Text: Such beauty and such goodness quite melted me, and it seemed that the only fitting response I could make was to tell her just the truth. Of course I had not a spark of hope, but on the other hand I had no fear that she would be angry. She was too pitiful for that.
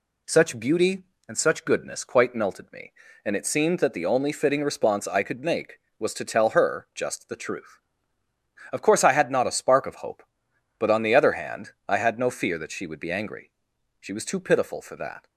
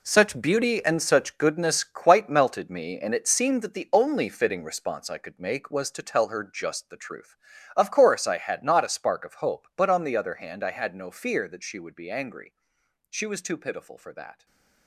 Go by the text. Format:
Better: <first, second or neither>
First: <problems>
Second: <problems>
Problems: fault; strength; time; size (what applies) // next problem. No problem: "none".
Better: first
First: none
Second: gets quieter; strong; throughout; 11 dB // stays silent after the last word; slight; from 14.3 s on; 0.5 s long